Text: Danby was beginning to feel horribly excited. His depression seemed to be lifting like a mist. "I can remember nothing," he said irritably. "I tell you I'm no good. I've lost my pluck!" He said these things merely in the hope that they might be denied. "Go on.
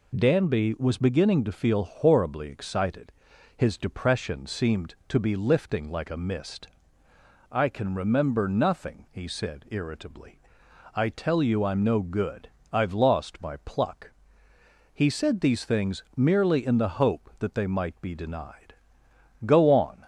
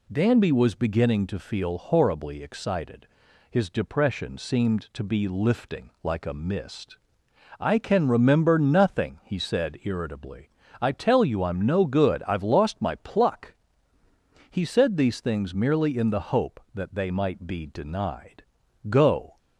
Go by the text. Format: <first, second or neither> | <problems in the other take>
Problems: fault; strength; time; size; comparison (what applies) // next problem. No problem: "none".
first | stops before "on"; at 19.3 s